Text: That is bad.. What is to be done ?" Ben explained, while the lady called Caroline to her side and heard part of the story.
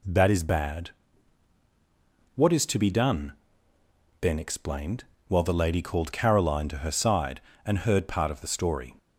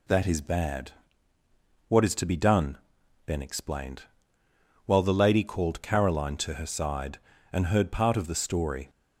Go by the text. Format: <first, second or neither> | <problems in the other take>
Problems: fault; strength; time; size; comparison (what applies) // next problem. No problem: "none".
neither | none